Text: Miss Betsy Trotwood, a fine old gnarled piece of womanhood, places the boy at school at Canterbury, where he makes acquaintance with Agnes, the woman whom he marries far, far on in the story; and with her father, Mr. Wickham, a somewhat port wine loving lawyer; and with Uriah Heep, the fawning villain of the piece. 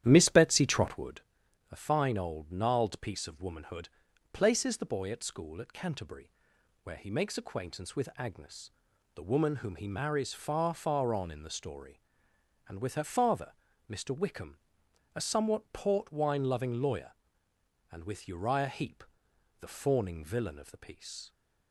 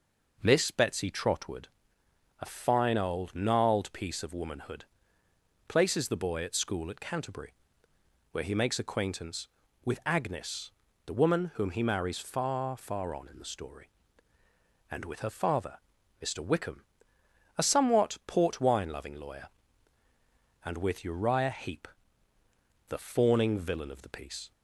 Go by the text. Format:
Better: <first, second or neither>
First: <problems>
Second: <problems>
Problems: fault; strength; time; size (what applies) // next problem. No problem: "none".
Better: second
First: starts louder than the rest; strong; until 1.2 s; 11 dB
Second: none